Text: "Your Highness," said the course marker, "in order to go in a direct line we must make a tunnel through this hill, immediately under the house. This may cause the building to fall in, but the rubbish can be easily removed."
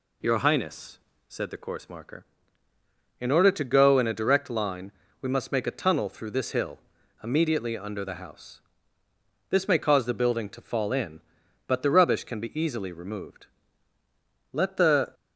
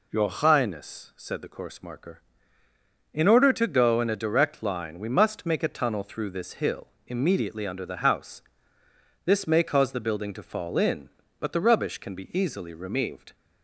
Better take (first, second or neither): second